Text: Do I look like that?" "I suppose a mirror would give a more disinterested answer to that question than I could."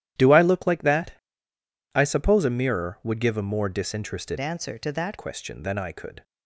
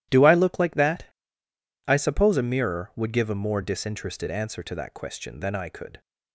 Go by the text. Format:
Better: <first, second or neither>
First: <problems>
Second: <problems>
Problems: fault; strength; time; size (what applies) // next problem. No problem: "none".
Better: second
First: starts louder than the rest; strong; until 1.9 s; 12 dB // changes voice from "answer" to "that"; from 4.3 to 5.1 s; 0.8 s long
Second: none